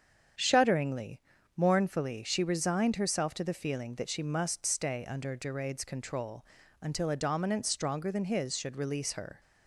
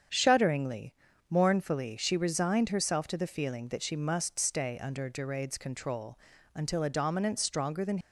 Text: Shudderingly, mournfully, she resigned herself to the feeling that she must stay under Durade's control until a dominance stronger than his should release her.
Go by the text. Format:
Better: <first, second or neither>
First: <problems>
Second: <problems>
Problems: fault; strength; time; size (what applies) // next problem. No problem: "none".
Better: first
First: starts louder than the rest; strong; until 1.7 s; 8 dB // pauses between "control" and "until"; at 6.4 s; 0.38 s long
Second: starts louder than the rest; strong; until 1.5 s; 8 dB // pauses between "control" and "until"; at 6.1 s; 0.38 s long // stops before "his should release her"; at 8.0 s